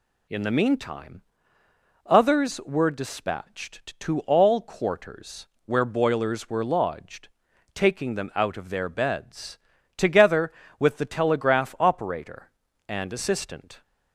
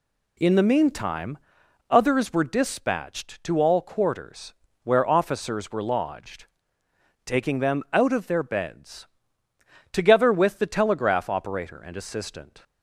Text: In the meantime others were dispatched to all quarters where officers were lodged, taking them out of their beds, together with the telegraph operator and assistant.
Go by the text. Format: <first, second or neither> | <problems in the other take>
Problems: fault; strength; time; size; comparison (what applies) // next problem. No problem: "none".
second | pauses between "meantime" and "others"; noticeable; at 1.2 s; 0.84 s long; noticeable in the second // pauses between "quarters" and "where"; slight; at 5.4 s; 0.20 s long; slight in the second // says "boilers" for "officers"; at 5.8 s